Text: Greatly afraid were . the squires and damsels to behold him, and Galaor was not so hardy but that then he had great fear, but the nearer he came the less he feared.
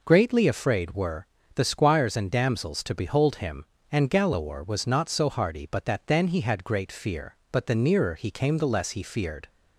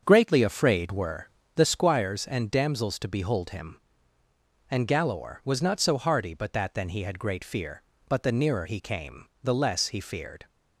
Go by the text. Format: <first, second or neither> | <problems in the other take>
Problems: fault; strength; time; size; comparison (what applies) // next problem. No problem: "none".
first | starts louder than the rest; until 1.7 s; 6.5 dB // pauses between "came" and "the"; slight; at 9.2 s; 0.16 s long